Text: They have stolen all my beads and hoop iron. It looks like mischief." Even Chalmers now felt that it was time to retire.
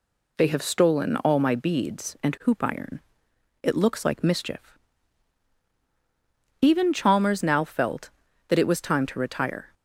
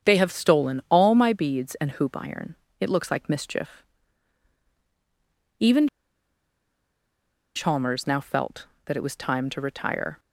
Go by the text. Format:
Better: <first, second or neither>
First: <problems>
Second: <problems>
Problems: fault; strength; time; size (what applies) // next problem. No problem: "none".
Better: first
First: none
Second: starts louder than the rest; strong; until 1.1 s; 8 dB // pauses between "Even" and "Chalmers"; strong; at 5.8 s; 1.6 s long